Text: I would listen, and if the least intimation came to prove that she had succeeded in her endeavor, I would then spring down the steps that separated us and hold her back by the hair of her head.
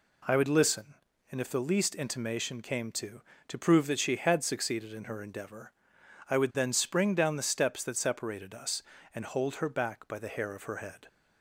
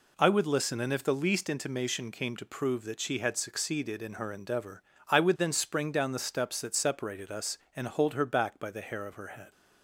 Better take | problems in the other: second | says "to" twice; at 3.4 s

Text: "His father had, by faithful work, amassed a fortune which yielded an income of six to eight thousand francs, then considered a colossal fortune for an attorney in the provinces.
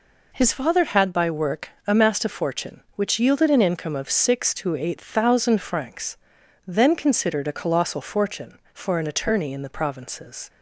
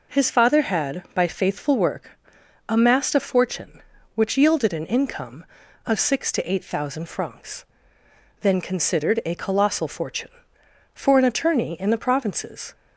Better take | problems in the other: second | skips "faithful"; at 1.2 s

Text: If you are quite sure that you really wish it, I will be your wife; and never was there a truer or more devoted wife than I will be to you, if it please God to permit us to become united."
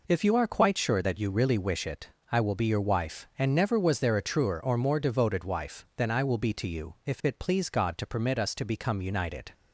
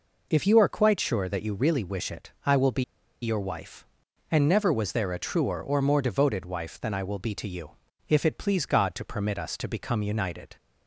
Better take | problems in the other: first | pauses between "be" and "your"; at 2.8 s; 0.40 s long

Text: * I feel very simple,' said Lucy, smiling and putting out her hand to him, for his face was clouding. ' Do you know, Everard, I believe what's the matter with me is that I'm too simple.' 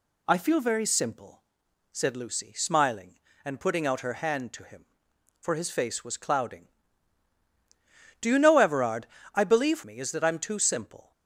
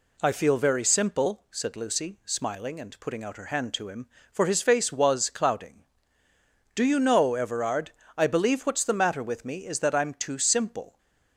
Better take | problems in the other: second | skips "what's the matter with"; at 9.8 s

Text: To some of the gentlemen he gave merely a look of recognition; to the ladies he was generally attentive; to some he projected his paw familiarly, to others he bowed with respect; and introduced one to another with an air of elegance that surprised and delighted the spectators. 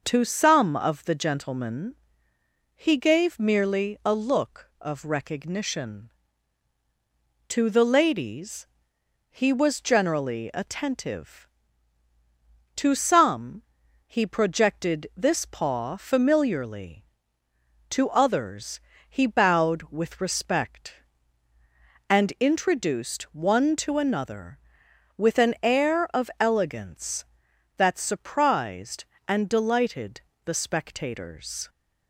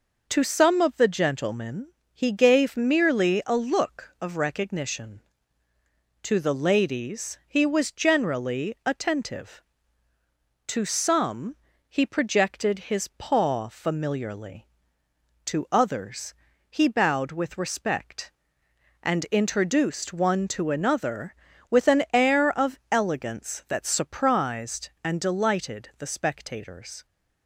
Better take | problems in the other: second | pauses between "gentlemen" and "he"; noticeable; at 1.9 s; 0.80 s long; slight in the second // pauses between "ladies" and "he"; noticeable; at 8.6 s; 0.62 s long // pauses between "some" and "he"; at 13.6 s; 0.42 s long; slight in the second // says "this" for "his"; at 15.1 s // pauses between "others" and "he"; slight; at 18.8 s; 0.28 s long; slight in the second // pauses between "delighted" and "the"; slight; at 30.1 s; 0.24 s long

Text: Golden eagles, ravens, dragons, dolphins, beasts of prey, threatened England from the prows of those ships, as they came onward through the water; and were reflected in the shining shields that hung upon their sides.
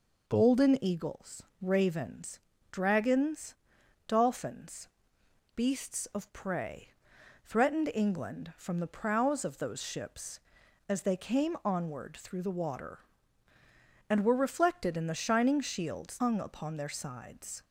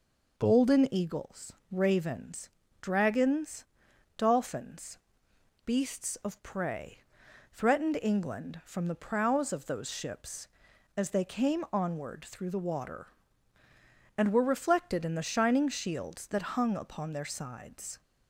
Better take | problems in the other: second | skips "that"; at 16.1 s

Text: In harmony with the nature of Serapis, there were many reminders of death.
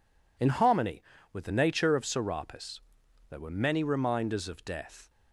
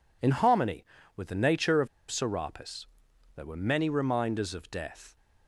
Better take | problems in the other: first | pauses between "of" and "Serapis"; slight; at 1.8 s; 0.23 s long

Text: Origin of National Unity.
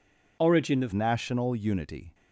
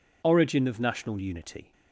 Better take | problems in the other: second | changes voice at "National"; from 0.9 s on; 1.2 s long

